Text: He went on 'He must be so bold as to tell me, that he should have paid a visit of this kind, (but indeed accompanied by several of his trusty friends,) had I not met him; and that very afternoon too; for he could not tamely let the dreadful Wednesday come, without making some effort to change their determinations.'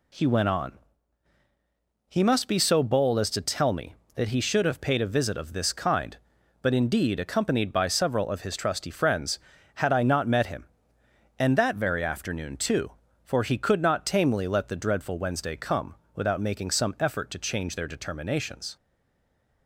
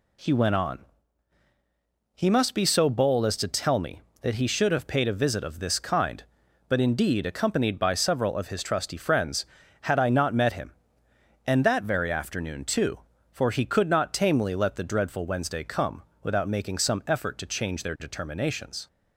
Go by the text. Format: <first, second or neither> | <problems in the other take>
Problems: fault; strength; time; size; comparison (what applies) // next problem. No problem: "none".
second | pauses between "on" and "He"; strong; at 0.7 s; 1.3 s long; strong in the second // stays silent after the last word; slight; from 18.7 s on; 0.9 s long